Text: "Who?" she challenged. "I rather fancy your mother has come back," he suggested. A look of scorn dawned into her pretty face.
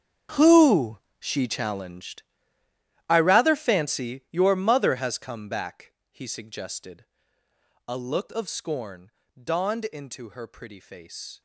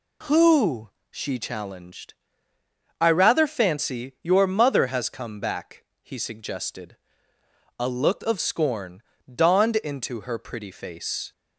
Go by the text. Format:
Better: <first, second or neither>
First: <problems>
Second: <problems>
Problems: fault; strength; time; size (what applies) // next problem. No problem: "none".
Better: second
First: gets quieter; strong; throughout; 16 dB // pauses between "scorn" and "dawned"; slight; at 9.1 s; 0.26 s long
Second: pauses between "scorn" and "dawned"; slight; at 9.0 s; 0.26 s long